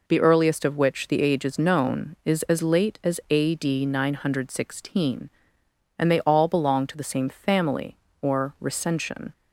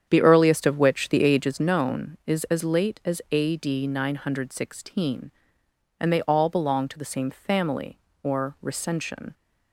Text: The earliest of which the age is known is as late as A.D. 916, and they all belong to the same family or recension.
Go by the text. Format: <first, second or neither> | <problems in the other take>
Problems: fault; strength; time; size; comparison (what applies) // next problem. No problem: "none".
first | starts louder than the rest; strong; until 1.7 s; 8.5 dB